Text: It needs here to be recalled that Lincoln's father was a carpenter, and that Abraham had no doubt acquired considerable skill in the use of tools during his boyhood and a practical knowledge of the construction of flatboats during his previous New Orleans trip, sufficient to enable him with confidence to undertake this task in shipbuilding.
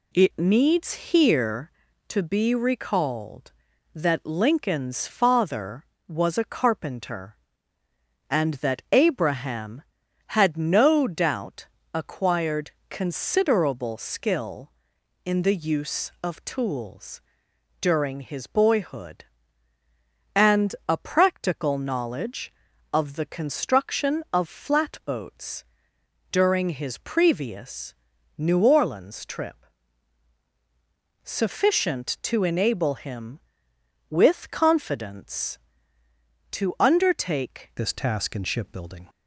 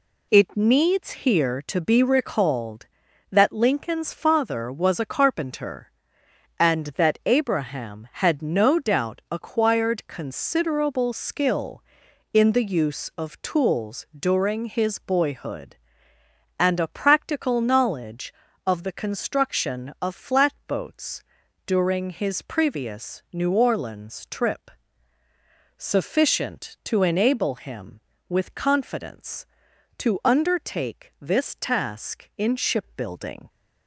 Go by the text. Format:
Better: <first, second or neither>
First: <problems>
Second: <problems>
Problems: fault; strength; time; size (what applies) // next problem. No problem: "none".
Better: second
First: pauses between "doubt" and "acquired"; slight; at 11.6 s; 0.26 s long // pauses between "acquired" and "considerable"; slight; at 12.7 s; 0.18 s long // pauses between "tools" and "during"; noticeable; at 17.2 s; 0.58 s long // pauses between "flatboats" and "during"; noticeable; at 25.6 s; 0.68 s long // pauses between "previous" and "New"; at 27.9 s; 0.44 s long // changes voice at "this"; from 37.7 s on; 1.3 s long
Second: pauses between "flatboats" and "during"; at 21.2 s; 0.42 s long